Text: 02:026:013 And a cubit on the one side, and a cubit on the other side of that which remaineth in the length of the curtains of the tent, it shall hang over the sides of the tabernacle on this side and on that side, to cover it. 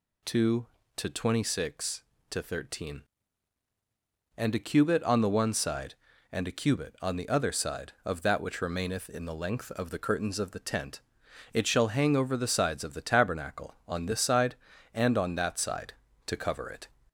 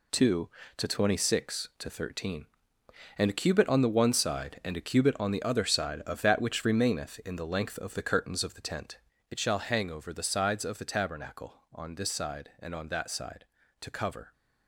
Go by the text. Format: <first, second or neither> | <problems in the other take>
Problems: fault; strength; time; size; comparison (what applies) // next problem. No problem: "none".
first | stops before "it"; at 14.3 s